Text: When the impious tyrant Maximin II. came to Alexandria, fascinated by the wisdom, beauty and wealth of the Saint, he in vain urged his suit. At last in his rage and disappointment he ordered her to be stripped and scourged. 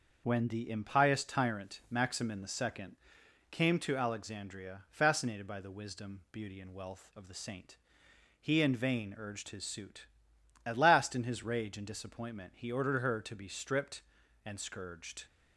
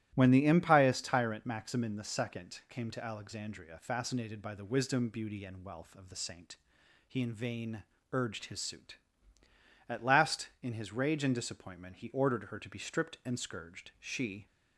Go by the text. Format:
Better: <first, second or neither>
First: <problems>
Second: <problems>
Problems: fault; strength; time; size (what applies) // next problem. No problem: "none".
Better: first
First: starts louder than the rest; noticeable; until 1.2 s; 6 dB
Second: starts louder than the rest; strong; until 1.1 s; 13.5 dB // pauses between "vain" and "urged"; slight; at 7.8 s; 0.30 s long // goes on to say "She"; slight; from 13.9 s on; 0.48 s long